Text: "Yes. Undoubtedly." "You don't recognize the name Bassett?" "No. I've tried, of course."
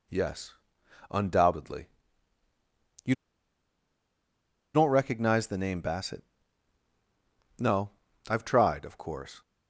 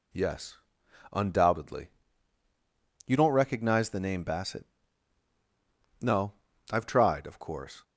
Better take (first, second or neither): second